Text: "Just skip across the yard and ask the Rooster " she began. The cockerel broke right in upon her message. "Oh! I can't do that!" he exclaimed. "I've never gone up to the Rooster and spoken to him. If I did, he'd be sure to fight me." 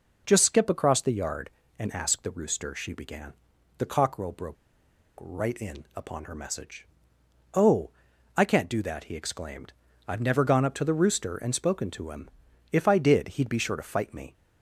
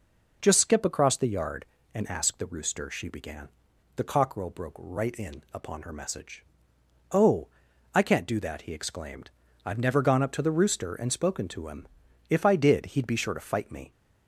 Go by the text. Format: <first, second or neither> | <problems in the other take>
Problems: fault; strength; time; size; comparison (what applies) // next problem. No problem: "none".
second | pauses between "broke" and "right"; noticeable; at 4.5 s; 0.65 s long